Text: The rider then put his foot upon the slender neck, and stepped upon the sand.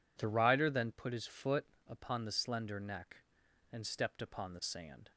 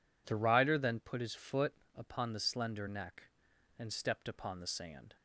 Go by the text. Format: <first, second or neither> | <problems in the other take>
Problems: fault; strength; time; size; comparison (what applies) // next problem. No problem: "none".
neither | pauses between "foot" and "upon"; slight; the same in both